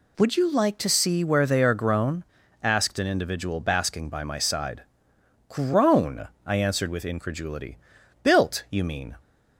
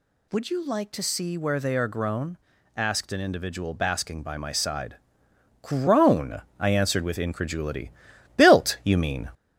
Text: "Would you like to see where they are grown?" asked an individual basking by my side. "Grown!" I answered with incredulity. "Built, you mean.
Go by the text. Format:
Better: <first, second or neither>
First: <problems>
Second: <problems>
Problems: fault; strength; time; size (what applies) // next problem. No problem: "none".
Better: first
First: none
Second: gets louder; slight; throughout; 3 dB